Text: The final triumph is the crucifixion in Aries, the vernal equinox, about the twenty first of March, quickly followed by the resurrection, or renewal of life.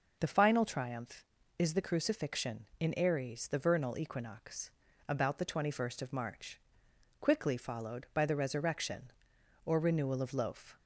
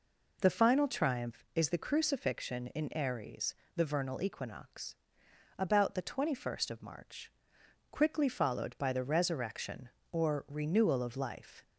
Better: second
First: says "loaf" for "life"; at 10.3 s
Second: none

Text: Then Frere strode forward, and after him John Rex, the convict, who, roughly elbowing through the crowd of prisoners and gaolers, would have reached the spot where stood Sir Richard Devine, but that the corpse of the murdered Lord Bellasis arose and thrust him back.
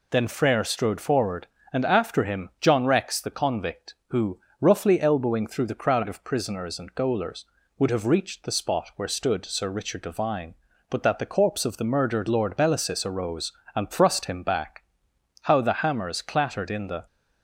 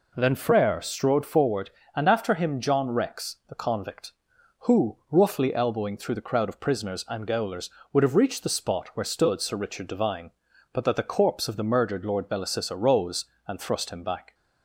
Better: second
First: goes on to say "How the hammers clattered in the"; from 15.4 s on; 1.6 s long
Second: none

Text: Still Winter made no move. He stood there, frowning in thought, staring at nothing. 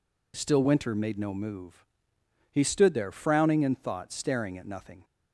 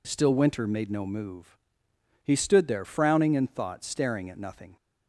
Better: neither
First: none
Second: none

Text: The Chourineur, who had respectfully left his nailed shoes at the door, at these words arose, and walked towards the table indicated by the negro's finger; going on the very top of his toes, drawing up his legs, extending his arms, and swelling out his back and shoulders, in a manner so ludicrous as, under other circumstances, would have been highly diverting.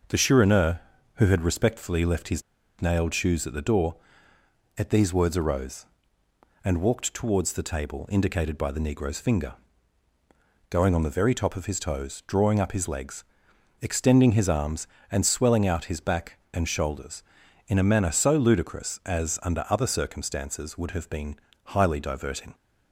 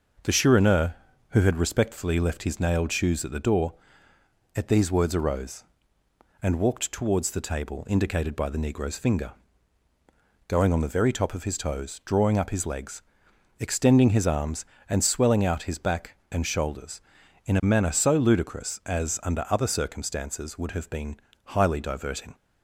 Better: second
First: pauses between "his" and "nailed"; at 2.4 s; 0.38 s long // pauses between "been" and "highly"; slight; at 21.3 s; 0.28 s long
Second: pauses between "been" and "highly"; slight; at 21.1 s; 0.28 s long

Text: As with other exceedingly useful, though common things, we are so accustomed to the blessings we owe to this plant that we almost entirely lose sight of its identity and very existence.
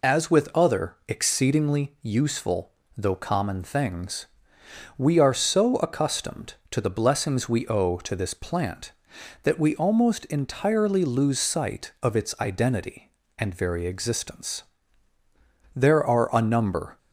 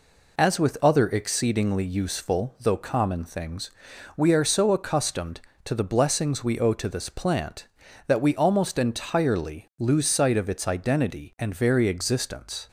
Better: second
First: goes on to say "There are a number"; noticeable; from 15.7 s on; 1.2 s long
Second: none

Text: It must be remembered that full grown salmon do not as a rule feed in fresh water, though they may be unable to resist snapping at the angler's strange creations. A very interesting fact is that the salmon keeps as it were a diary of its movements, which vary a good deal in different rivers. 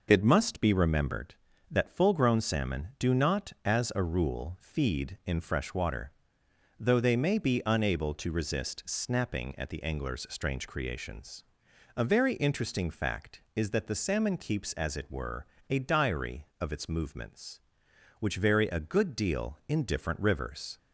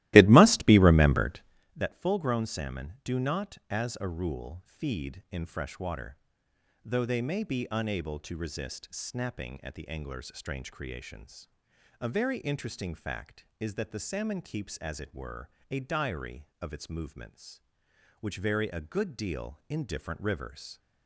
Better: first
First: pauses between "were" and "a"; slight; at 15.4 s; 0.24 s long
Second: starts louder than the rest; strong; until 1.7 s; 16.5 dB // pauses between "were" and "a"; slight; at 15.4 s; 0.22 s long

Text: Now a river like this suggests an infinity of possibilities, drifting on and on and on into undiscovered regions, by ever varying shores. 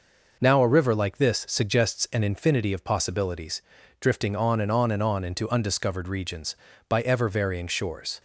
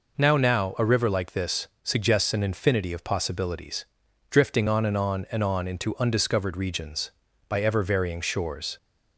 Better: first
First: none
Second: says "Now" twice; at 0.3 s // pauses between "this" and "suggests"; slight; at 1.6 s; 0.16 s long

